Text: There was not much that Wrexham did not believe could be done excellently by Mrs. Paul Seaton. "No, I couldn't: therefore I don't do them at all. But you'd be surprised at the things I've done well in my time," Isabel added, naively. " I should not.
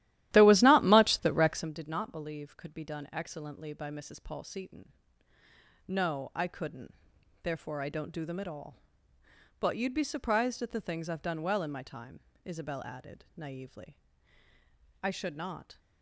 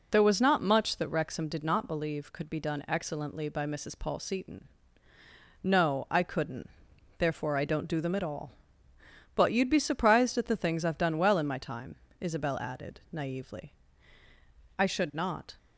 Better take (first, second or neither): second